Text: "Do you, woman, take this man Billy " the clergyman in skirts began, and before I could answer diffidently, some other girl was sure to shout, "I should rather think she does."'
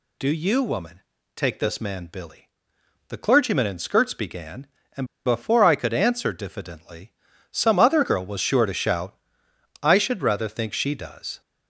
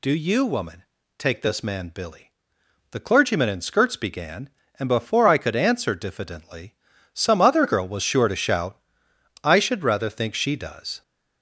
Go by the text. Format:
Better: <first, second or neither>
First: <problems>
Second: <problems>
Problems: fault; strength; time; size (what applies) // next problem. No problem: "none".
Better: second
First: pauses between "and" and "before"; slight; at 5.0 s; 0.20 s long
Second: none